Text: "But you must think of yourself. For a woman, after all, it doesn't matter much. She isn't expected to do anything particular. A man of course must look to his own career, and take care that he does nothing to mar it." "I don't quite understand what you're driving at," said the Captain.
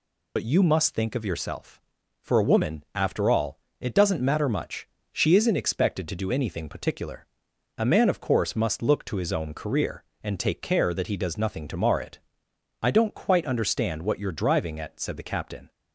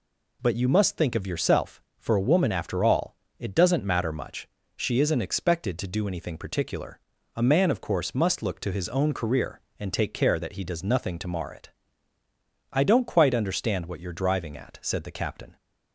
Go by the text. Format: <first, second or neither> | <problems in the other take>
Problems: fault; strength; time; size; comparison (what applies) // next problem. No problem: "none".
second | loses the start of "But"; at 0.3 s; 60 ms